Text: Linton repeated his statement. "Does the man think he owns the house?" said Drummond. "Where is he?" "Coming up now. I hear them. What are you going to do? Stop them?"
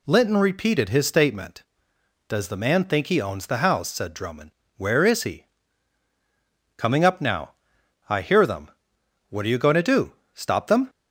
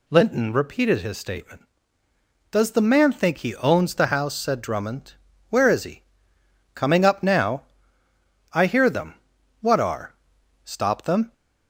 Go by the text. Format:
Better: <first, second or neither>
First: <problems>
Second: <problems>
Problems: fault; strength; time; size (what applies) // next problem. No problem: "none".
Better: first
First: none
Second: skips "you going to do"; at 10.3 s